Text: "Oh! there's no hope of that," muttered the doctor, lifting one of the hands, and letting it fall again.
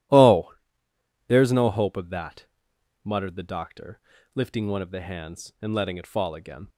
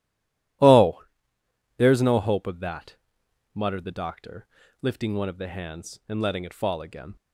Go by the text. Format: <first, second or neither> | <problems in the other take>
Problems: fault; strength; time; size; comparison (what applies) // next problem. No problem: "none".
first | stays silent before the first word; slight; until 0.6 s; 0.6 s long